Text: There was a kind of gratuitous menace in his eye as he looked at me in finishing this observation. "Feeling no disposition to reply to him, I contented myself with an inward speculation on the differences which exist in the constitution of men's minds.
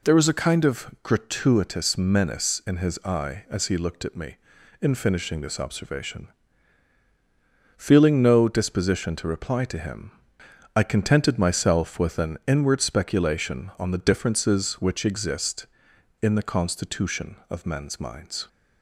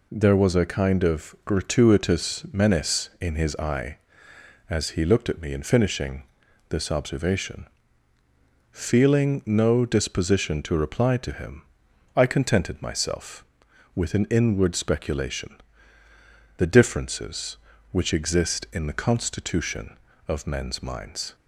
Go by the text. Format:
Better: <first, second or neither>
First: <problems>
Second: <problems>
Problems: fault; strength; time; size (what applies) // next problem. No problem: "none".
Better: first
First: none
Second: pauses between "finishing" and "this"; noticeable; at 6.2 s; 0.48 s long // skips "on"; at 16.0 s